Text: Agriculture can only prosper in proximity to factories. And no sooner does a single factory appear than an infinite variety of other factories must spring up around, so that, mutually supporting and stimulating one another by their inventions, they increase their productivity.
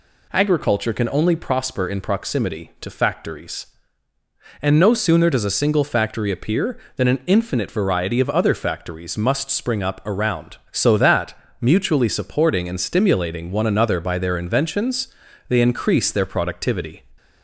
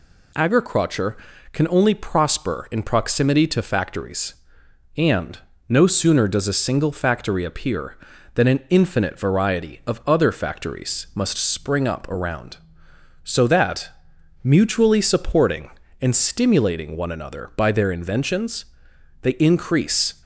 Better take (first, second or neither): first